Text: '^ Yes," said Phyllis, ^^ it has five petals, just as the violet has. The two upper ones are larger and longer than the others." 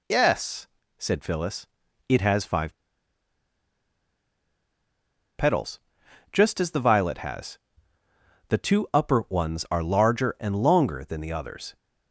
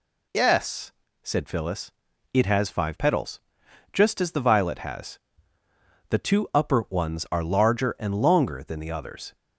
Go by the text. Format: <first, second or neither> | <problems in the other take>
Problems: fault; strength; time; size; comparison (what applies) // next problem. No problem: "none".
second | pauses between "five" and "petals"; strong; at 2.7 s; 2.6 s long